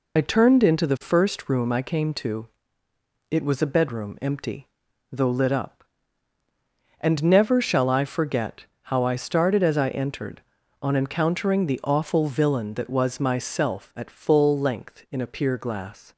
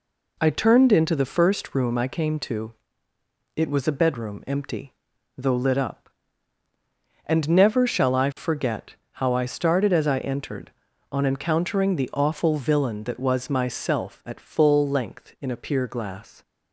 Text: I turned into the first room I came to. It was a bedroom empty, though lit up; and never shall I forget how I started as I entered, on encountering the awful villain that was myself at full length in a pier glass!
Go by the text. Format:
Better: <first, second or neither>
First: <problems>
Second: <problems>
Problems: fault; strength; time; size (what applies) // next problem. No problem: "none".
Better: second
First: loses the start of "I"; at 0.1 s; 50 ms // pauses between "forget" and "how"; slight; at 8.6 s; 0.16 s long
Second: pauses between "forget" and "how"; slight; at 8.9 s; 0.16 s long